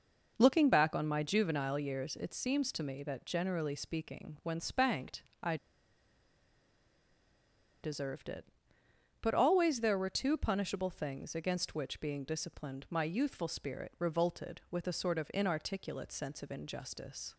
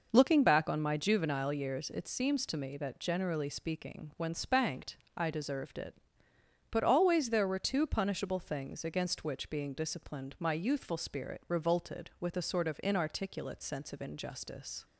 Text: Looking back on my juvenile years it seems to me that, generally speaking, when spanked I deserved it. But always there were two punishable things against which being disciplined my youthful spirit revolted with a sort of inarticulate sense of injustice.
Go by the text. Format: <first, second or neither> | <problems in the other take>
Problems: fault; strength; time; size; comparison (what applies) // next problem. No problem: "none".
second | pauses between "spanked" and "I"; slight; at 5.2 s; 0.20 s long; slight in the second // pauses between "I" and "deserved"; strong; at 5.5 s; 2.2 s long